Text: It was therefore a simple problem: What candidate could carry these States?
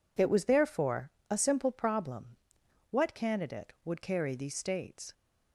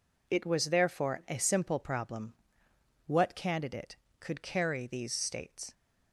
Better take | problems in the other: second | pauses between "therefore" and "a"; slight; at 1.1 s; 0.18 s long // says "would" for "could"; at 3.8 s

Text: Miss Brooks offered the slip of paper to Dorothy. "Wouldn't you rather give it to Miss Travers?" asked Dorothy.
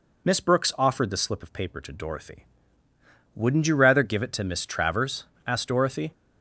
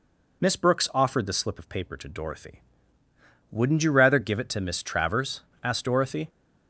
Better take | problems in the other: neither | none

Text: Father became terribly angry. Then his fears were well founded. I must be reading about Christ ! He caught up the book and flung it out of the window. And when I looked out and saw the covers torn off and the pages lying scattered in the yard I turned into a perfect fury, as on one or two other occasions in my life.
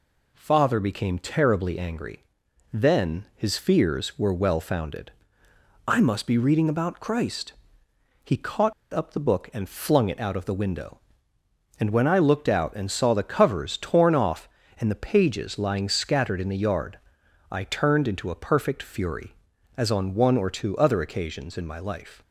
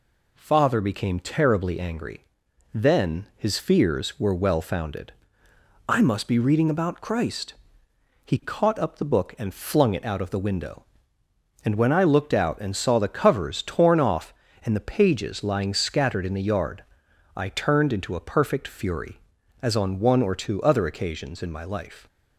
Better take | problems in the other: second | pauses between "caught" and "up"; slight; at 8.7 s; 0.21 s long // pauses between "yard" and "I"; noticeable; at 16.9 s; 0.52 s long; noticeable in the second

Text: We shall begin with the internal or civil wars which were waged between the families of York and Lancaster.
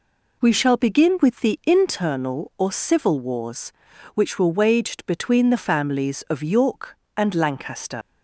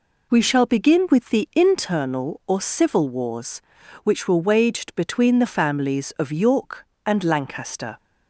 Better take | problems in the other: second | leaves "Lancaster" unfinished; at 8.0 s; 60 ms

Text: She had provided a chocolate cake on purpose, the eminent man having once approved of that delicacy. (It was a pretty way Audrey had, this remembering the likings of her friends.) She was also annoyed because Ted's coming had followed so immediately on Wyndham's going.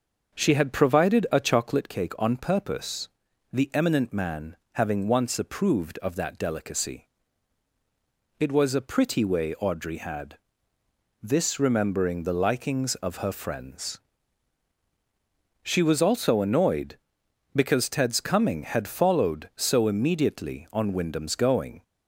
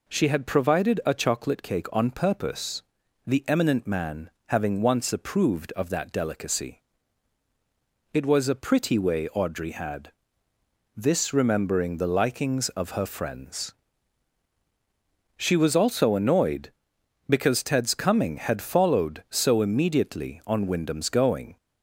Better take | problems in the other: second | starts louder than the rest; until 1.9 s; 7 dB // pauses between "man" and "having"; slight; at 4.5 s; 0.16 s long; slight in the second

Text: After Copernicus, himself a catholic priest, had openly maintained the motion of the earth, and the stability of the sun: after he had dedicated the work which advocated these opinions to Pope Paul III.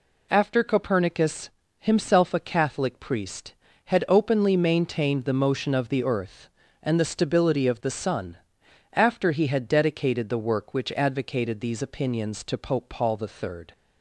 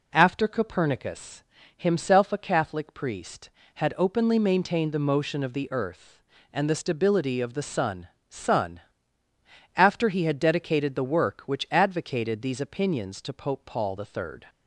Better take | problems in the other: first | says "sun" twice; at 8.3 s

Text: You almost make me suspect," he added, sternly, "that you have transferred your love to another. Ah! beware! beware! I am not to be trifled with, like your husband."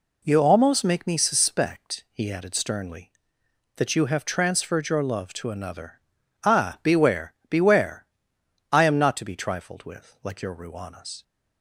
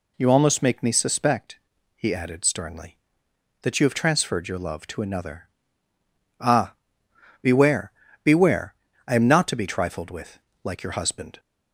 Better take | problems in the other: second | says "ruanas" for "husband"; at 10.5 s

